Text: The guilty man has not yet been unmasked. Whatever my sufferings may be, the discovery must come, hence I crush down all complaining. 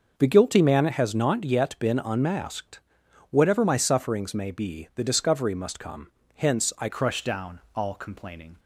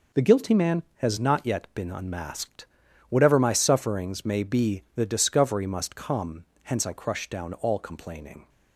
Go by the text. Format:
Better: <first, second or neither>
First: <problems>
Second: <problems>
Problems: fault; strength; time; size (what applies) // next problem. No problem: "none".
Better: second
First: changes voice at "crush"; from 6.8 s on; 1.7 s long // pauses between "down" and "all"; slight; at 7.5 s; 0.16 s long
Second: none